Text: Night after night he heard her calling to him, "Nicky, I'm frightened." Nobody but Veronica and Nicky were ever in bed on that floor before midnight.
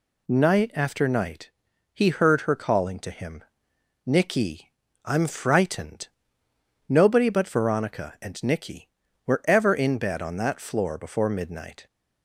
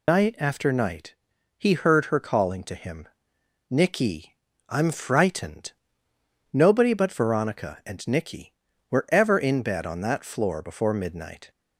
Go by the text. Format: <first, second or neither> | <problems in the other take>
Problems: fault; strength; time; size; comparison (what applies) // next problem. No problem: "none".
first | loses the start of "Night"; at 0.0 s; 160 ms // pauses between "night" and "he"; at 1.1 s; 0.44 s long; also in the first